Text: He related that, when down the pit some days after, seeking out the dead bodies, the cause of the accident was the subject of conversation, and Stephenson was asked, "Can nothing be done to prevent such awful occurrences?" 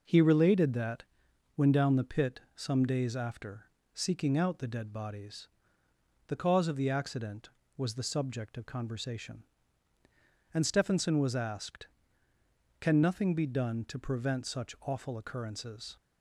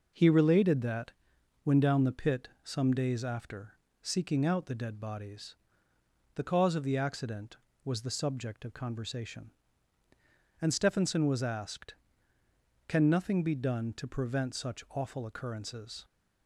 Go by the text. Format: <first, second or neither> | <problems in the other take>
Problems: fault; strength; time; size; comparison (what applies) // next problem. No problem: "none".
neither | none